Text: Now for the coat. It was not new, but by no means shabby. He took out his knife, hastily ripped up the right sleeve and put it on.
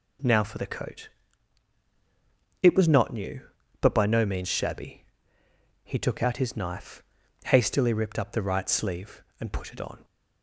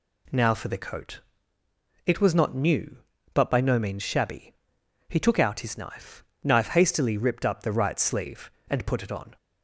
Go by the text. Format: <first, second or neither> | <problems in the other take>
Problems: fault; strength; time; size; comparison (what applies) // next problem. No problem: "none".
first | says "knife" twice; at 6.4 s